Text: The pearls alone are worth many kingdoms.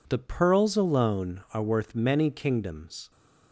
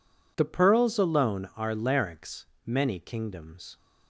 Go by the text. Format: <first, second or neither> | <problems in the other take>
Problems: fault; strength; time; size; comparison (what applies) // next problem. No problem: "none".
first | says "larynx" for "worth"; at 1.7 s